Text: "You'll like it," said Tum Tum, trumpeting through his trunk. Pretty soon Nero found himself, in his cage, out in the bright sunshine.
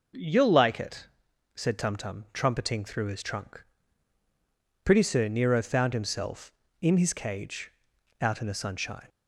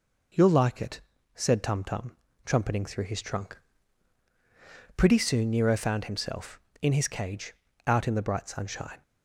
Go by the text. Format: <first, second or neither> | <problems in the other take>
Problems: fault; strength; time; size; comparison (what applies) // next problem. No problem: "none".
second | skips "bright"; at 8.5 s